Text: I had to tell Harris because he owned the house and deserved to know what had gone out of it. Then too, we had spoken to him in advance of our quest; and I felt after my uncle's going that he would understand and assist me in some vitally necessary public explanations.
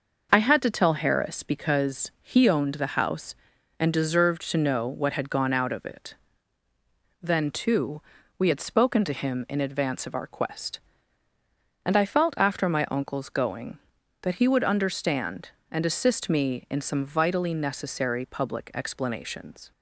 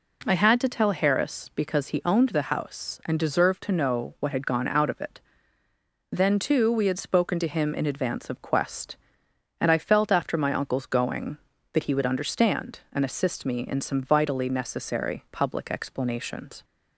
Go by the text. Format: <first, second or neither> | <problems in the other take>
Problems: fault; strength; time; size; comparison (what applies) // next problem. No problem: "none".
first | skips "our"; at 8.3 s